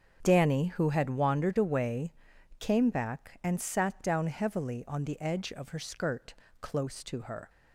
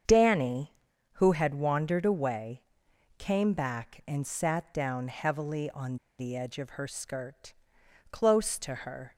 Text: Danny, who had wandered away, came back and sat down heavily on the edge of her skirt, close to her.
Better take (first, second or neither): first